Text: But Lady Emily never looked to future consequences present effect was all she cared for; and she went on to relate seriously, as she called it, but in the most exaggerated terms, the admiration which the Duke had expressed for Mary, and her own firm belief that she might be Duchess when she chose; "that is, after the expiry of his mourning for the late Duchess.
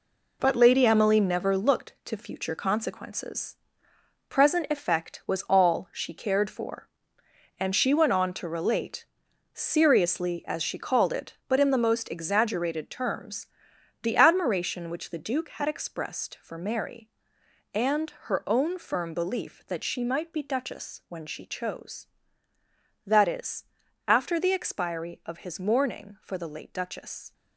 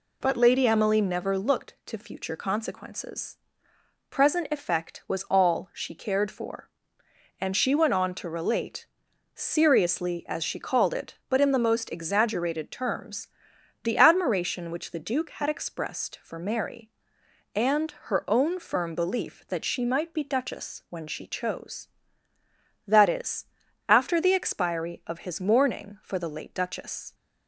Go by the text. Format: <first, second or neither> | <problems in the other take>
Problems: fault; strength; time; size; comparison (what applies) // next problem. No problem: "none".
second | gets quieter; strong; throughout; 9 dB // pauses between "consequences" and "present"; noticeable; at 3.5 s; 0.74 s long; noticeable in the second // pauses between "relate" and "seriously"; noticeable; at 9.0 s; 0.48 s long; noticeable in the second // pauses between "and" and "her"; slight; at 18.1 s; 0.20 s long; slight in the second